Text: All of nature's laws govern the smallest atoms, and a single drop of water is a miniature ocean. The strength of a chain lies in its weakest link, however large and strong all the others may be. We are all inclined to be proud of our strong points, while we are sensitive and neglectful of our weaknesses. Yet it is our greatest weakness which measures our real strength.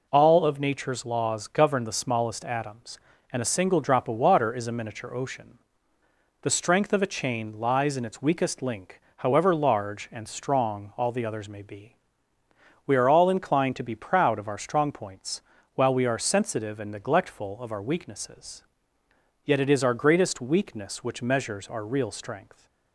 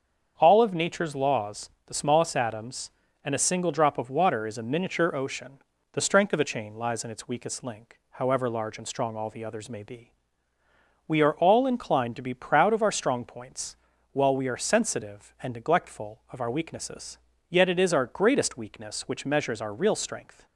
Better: first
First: none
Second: starts louder than the rest; strong; until 1.3 s; 7 dB // skips "govern"; at 1.7 s

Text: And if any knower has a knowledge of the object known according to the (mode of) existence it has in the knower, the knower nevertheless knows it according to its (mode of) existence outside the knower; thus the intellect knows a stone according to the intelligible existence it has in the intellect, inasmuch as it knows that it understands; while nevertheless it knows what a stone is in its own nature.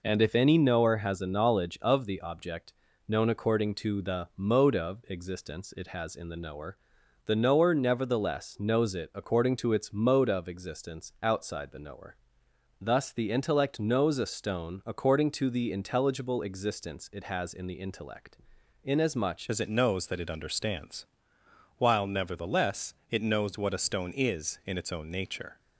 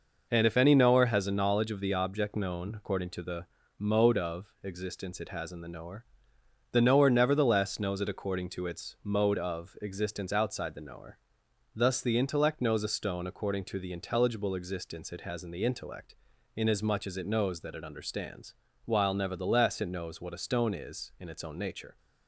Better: second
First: pauses between "object" and "known"; slight; at 2.7 s; 0.34 s long // changes voice at "as"; from 19.5 s on; 6.0 s long // pauses between "nevertheless" and "it"; slight; at 22.9 s; 0.16 s long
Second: none

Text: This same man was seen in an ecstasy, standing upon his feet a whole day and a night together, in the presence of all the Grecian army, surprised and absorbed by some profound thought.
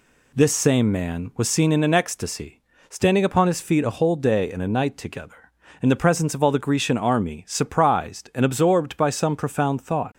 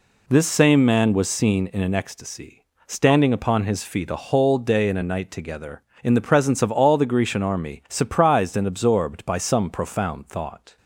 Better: neither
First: none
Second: none

